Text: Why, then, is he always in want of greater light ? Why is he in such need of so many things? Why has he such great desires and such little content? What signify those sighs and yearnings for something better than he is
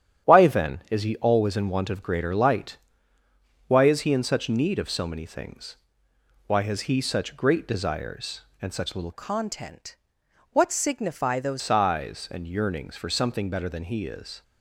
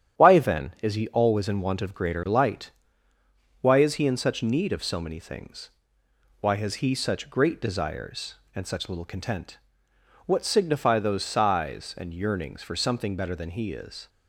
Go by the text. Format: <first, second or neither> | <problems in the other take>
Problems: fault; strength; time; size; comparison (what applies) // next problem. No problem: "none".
second | starts louder than the rest; strong; until 1.3 s; 9.5 dB; strong in the second // changes voice from "content" to "those"; from 9.1 to 11.6 s; 2.5 s long